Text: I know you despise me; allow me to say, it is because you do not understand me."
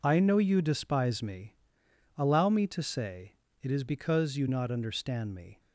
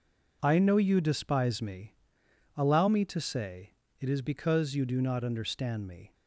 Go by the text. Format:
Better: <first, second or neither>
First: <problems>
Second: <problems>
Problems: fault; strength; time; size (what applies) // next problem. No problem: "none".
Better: second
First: skips "do"; at 4.4 s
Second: none